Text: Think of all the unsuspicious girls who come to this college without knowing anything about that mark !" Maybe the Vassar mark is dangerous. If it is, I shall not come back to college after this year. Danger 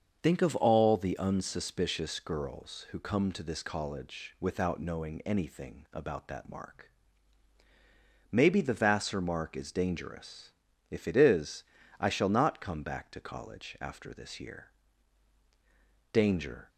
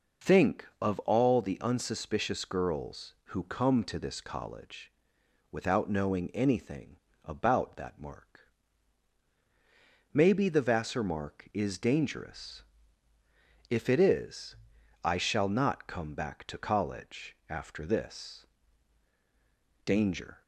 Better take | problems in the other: first | starts louder than the rest; strong; until 1.3 s; 7.5 dB; also in the first // pauses between "college" and "without"; noticeable; at 4.9 s; 0.58 s long // pauses between "anything" and "about"; slight; at 6.9 s; 0.26 s long // skips "year"; at 19.1 s

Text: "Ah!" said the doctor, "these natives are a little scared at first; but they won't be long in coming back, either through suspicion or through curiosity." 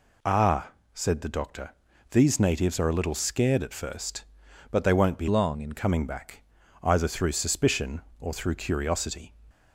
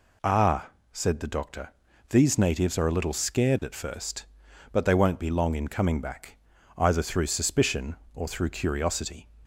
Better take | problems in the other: second | changes voice from "long" to "in"; from 5.2 to 5.7 s; 0.5 s long

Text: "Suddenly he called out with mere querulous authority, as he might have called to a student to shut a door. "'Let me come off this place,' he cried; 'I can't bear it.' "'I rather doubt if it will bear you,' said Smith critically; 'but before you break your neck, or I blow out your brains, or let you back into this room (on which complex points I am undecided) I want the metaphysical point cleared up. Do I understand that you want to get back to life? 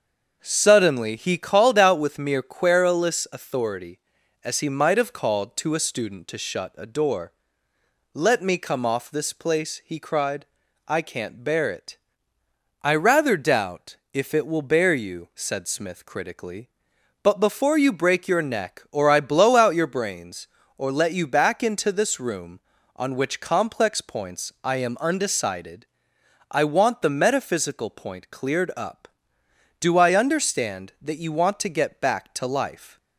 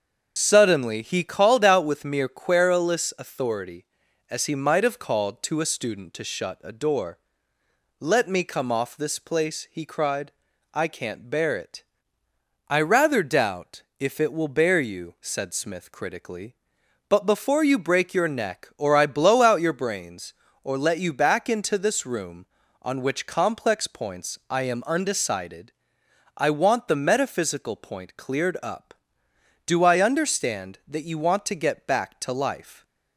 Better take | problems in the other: first | loses the start of "Suddenly"; at 0.3 s; 85 ms // starts louder than the rest; until 1.3 s; 6.5 dB; also in the first // pauses between "doubt" and "if"; slight; at 13.8 s; 0.16 s long; slight in the first

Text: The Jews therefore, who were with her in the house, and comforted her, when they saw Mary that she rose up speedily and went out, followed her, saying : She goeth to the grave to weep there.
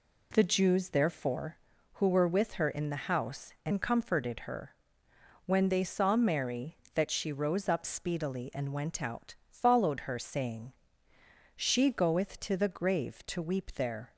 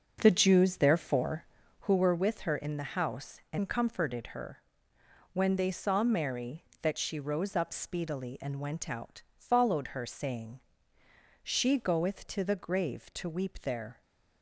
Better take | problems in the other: first | starts louder than the rest; until 2.1 s; 6 dB

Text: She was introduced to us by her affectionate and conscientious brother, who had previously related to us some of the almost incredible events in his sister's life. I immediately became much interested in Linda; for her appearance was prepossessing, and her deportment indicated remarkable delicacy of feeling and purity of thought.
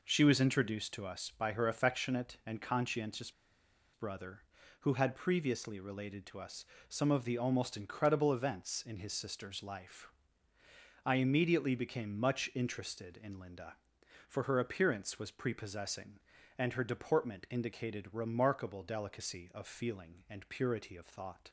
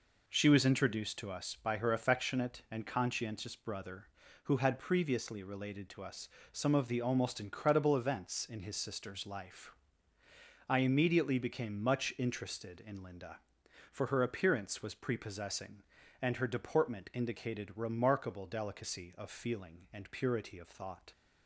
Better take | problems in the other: second | pauses between "conscientious" and "brother"; noticeable; at 3.3 s; 0.62 s long // pauses between "us" and "some"; slight; at 6.6 s; 0.22 s long; slight in the second

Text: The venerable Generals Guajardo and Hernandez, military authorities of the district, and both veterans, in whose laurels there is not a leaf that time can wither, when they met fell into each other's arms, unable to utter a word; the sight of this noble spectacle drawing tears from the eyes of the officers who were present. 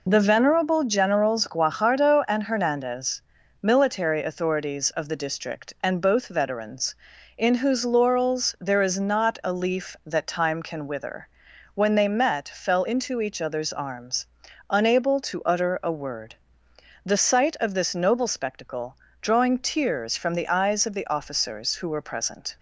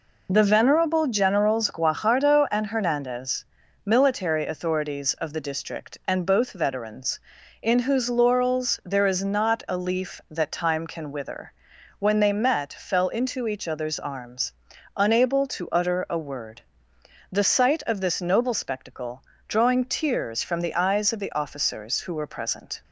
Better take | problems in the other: neither | pauses between "spectacle" and "drawing"; slight; the same in both

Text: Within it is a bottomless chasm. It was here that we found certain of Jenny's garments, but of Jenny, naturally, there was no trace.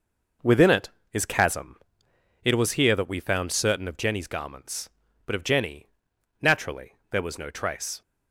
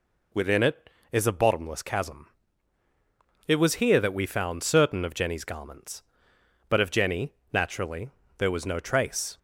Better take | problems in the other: second | skips "a bottomless"; at 1.2 s

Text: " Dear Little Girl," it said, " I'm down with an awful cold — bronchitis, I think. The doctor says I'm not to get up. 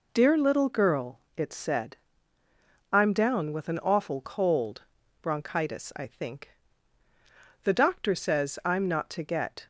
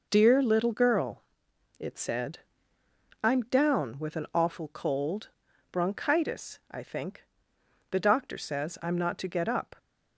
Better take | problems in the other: second | stops before "up"; at 9.6 s

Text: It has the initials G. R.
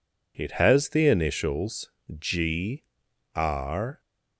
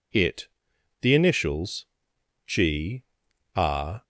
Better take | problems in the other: first | skips "has"; at 0.7 s // pauses between "initials" and "G"; noticeable; at 1.8 s; 0.62 s long; slight in the first // pauses between "G" and "R"; noticeable; at 3.0 s; 0.52 s long; noticeable in the first

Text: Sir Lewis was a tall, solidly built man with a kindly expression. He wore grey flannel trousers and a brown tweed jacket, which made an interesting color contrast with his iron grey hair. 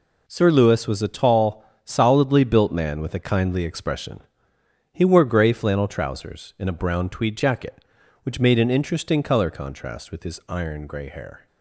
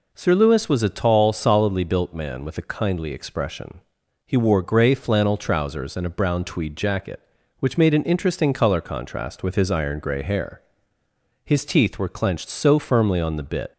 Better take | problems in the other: first | goes on to say "His teeth were clenched so firmly on the bit"; strong; from 11.4 s on; 2.2 s long

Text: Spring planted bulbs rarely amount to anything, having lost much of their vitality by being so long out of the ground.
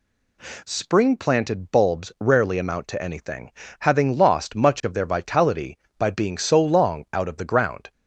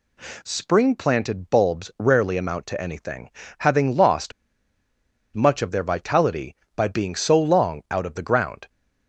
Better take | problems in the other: first | pauses between "lost" and "much"; at 4.3 s; 1.0 s long

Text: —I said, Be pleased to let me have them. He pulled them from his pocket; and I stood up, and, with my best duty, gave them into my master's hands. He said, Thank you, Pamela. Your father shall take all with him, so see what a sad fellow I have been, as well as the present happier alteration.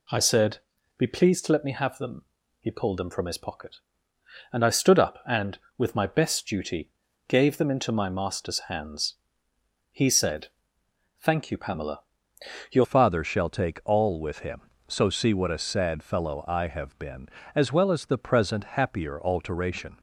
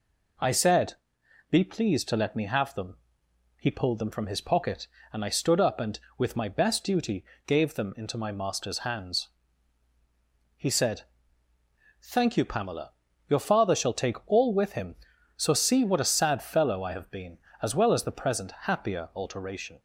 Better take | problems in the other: second | changes voice at "father"; from 12.8 s on; 7.1 s long

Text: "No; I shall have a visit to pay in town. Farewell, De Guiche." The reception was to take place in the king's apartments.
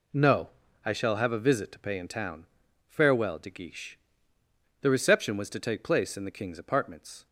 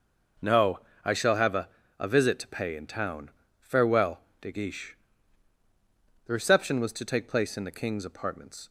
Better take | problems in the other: first | says "a" twice; at 1.9 s

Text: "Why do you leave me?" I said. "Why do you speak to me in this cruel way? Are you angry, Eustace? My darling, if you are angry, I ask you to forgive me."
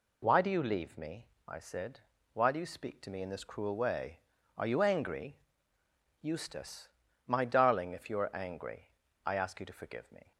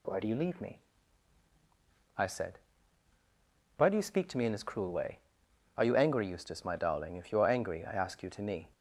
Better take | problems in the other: first | skips "forgive"; at 8.4 s

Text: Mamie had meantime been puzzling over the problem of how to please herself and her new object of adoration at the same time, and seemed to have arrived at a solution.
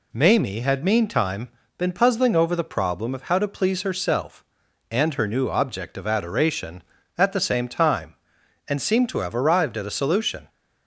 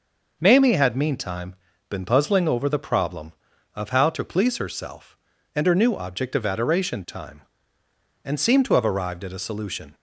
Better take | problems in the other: first | pauses between "meantime" and "been"; slight; at 1.5 s; 0.34 s long; slight in the first // skips "at the same"; at 7.0 s

